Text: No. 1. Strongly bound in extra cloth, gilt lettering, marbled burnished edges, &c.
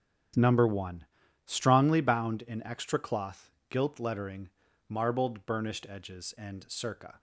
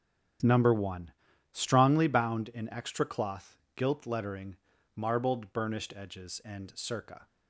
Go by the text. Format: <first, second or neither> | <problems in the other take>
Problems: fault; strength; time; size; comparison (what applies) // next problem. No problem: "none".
neither | starts louder than the rest; strong; the same in both